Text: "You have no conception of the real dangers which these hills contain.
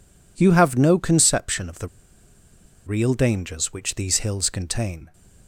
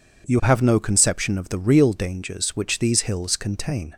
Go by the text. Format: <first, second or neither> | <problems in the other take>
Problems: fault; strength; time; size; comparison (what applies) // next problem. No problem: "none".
second | pauses between "the" and "real"; at 1.8 s; 0.98 s long